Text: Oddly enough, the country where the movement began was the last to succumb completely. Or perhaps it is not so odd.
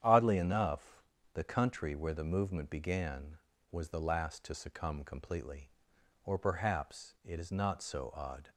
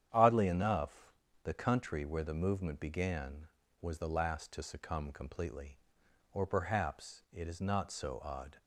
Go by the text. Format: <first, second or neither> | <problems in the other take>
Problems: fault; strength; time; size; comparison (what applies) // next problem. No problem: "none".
neither | starts louder than the rest; strong; the same in both